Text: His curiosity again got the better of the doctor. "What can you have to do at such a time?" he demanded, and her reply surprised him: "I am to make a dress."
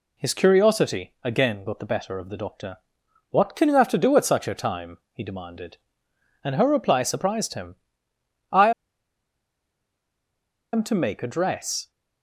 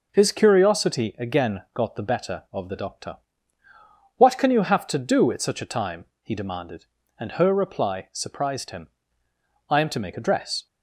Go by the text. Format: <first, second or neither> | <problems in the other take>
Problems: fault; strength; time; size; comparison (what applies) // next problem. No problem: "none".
second | pauses between "I" and "am"; strong; at 8.7 s; 2.0 s long